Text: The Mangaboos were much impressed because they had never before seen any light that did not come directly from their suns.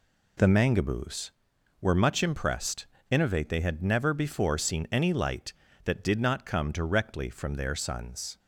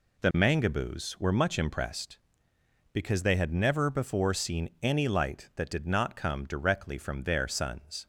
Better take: second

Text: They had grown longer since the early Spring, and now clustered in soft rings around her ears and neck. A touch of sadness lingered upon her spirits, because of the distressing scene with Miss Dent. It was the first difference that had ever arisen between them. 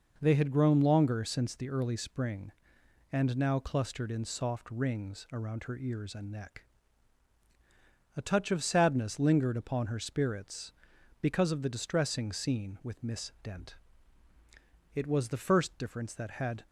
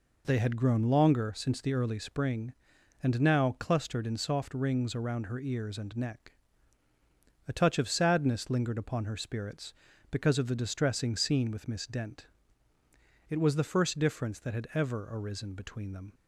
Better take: second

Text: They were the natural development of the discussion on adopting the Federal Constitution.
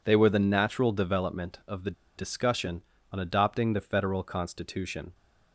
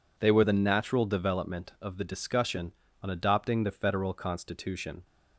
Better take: second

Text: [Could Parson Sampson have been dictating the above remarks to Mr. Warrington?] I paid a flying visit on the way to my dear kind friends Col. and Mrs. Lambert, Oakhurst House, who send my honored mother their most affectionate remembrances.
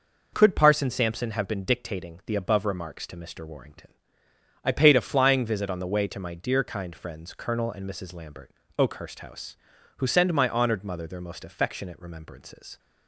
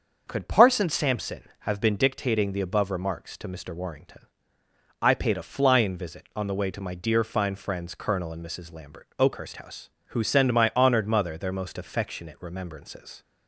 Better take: first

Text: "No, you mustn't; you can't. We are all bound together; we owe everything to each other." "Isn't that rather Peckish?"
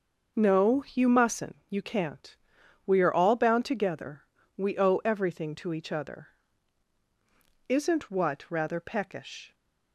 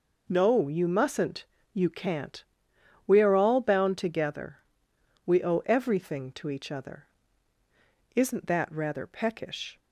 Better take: second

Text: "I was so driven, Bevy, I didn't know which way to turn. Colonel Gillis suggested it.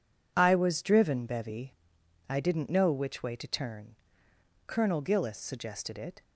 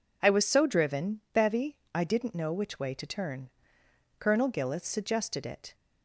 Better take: second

